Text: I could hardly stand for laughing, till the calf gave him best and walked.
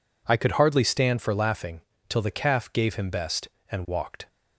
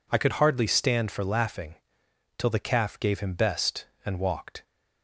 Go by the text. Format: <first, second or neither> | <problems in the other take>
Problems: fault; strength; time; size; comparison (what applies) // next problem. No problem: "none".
neither | none